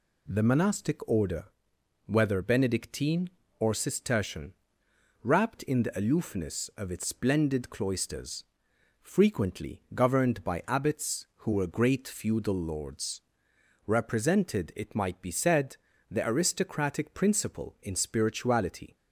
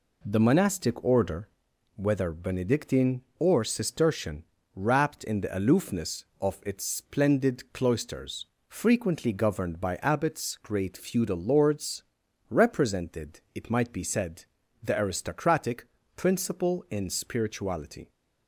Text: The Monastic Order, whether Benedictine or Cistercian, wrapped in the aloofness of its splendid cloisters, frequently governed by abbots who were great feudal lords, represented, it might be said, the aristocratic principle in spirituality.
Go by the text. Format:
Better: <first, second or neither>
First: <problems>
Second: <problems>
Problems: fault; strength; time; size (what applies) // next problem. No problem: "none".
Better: first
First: none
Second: skips "who were"; at 10.6 s // pauses between "aristocratic" and "principle"; slight; at 15.8 s; 0.30 s long